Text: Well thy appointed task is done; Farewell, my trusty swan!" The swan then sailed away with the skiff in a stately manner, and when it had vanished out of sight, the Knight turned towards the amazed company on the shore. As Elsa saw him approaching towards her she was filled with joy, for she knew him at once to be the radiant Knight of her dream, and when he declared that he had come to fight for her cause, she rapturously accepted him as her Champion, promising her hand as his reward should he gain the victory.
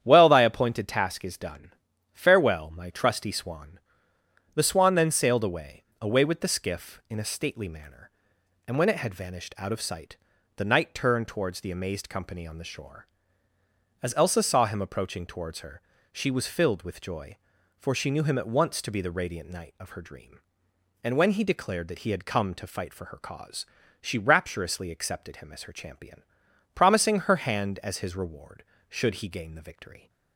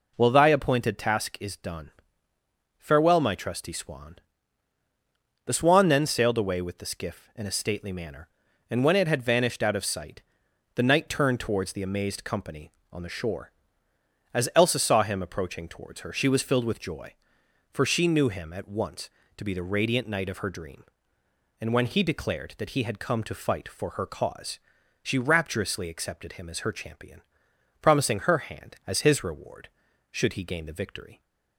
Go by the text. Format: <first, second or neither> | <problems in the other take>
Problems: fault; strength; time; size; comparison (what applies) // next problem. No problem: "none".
second | starts louder than the rest; strong; until 1.0 s; 9.5 dB // says "away" twice; at 6.0 s // pauses between "her" and "she"; slight; at 15.8 s; 0.28 s long